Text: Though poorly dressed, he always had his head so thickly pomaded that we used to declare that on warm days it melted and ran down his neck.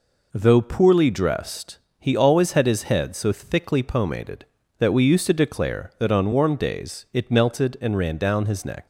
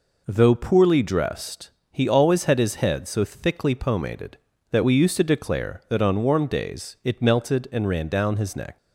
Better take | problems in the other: neither | none

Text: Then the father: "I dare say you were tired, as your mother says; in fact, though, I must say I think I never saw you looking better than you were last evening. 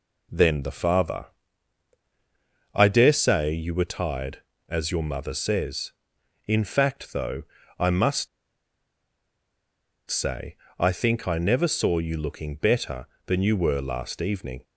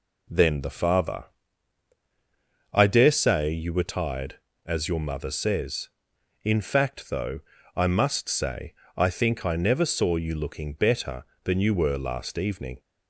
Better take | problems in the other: second | pauses between "must" and "say"; strong; at 8.2 s; 1.8 s long // pauses between "say" and "I"; slight; at 10.5 s; 0.24 s long; slight in the second

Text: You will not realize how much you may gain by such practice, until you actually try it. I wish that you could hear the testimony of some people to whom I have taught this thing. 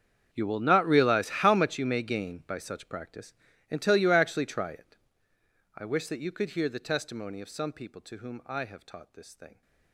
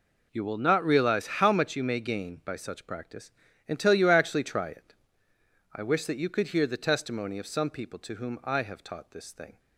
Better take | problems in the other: second | gets quieter; strong; throughout; 20 dB

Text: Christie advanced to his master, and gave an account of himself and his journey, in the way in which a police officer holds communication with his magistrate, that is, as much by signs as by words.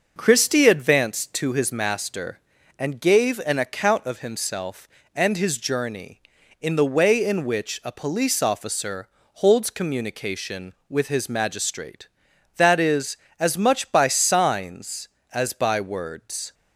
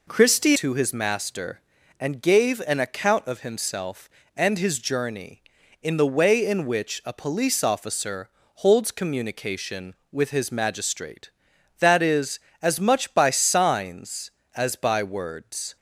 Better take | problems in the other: first | skips "advanced"; at 0.5 s // pauses between "officer" and "holds"; slight; at 8.2 s; 0.28 s long; slight in the first

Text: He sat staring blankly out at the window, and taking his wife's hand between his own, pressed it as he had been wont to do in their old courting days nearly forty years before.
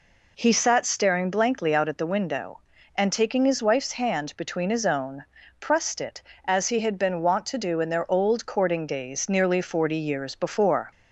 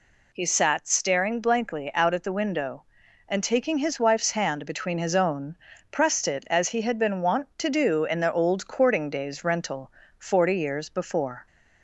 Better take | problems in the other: first | says "rental" for "nearly"; at 9.4 s

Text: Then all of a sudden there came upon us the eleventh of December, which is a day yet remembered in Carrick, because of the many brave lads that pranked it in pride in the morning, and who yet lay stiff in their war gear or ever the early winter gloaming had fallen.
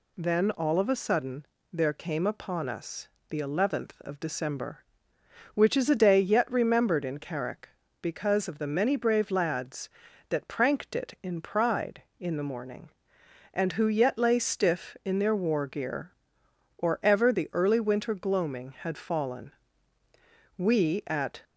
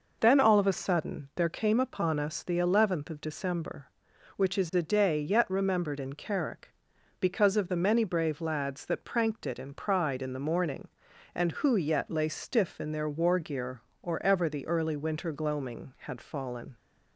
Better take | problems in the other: second | pauses between "sudden" and "there"; slight; at 1.4 s; 0.26 s long // pauses between "us" and "the"; slight; at 3.0 s; 0.22 s long // goes on to say "We at"; noticeable; from 20.5 s on; 0.86 s long

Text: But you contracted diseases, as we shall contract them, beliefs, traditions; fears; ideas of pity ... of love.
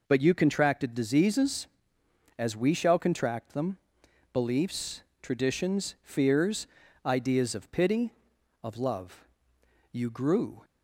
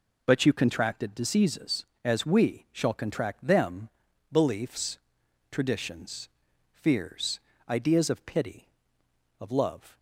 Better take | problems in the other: second | goes on to say "You grew"; noticeable; from 9.9 s on; 0.72 s long

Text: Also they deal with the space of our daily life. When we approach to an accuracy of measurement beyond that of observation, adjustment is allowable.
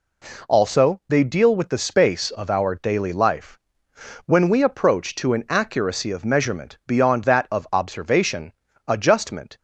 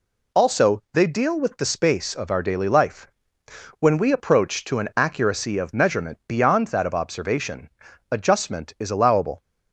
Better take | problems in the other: second | stops before "is allowable"; at 9.5 s

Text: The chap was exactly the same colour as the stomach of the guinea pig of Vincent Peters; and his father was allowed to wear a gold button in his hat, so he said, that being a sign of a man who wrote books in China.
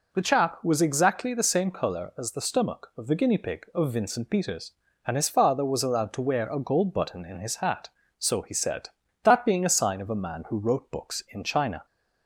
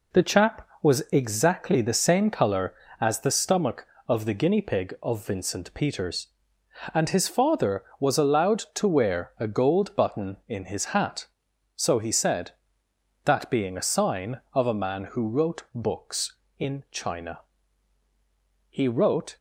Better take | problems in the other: first | goes on to say "He wrote"; noticeable; from 18.6 s on; 0.68 s long

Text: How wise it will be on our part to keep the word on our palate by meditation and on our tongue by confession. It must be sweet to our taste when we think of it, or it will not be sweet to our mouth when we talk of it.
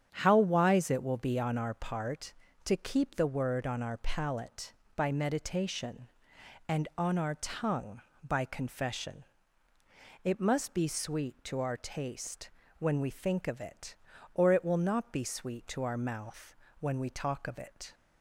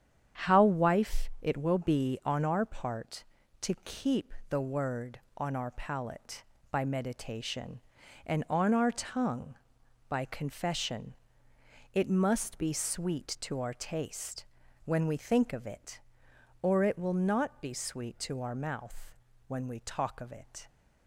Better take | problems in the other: first | starts louder than the rest; strong; until 1.5 s; 9 dB; strong in the first // says "wife" for "wise"; at 0.6 s // pauses between "keep" and "the"; slight; at 4.3 s; 0.16 s long // pauses between "taste" and "when"; at 14.4 s; 0.40 s long; slight in the first // pauses between "mouth" and "when"; slight; at 19.1 s; 0.34 s long; slight in the first

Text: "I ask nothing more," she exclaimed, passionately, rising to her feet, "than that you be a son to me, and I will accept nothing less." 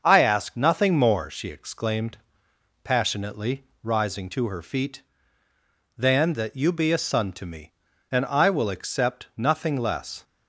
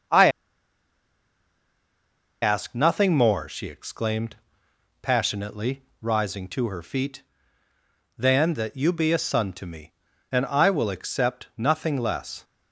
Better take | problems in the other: first | starts louder than the rest; until 3.2 s; 6.5 dB; also in the first // pauses between "I" and "ask"; strong; at 0.2 s; 2.1 s long

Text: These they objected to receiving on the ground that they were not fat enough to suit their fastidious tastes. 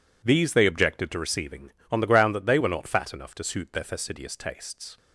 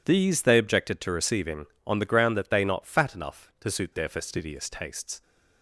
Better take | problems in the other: first | skips "were"; at 2.6 s

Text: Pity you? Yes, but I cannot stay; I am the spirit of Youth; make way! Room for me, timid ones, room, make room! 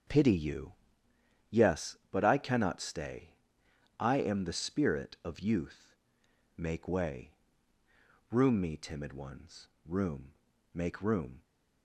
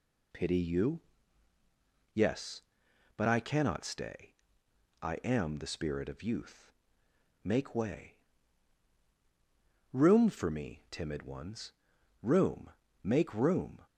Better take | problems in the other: second | starts louder than the rest; strong; until 1.8 s; 7 dB // skips "for"; at 8.5 s

